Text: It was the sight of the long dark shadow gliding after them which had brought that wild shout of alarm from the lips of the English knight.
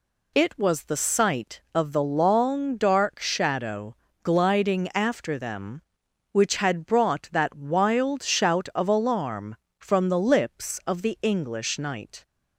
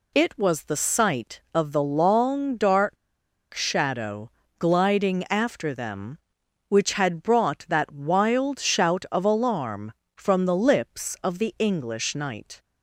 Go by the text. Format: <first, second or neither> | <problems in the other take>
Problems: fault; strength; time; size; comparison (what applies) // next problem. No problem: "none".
first | pauses between "dark" and "shadow"; noticeable; at 2.9 s; 0.58 s long // pauses between "shadow" and "gliding"; slight; at 4.3 s; 0.28 s long; slight in the first